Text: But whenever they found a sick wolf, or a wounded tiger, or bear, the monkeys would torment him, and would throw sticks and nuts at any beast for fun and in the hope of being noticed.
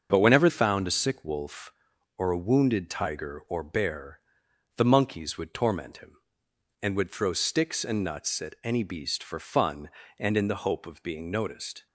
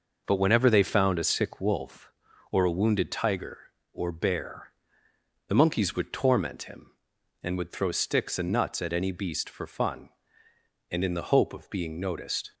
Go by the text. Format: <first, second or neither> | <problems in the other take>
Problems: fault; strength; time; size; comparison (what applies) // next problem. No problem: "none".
second | starts louder than the rest; until 1.1 s; 7 dB // skips "they"; at 0.4 s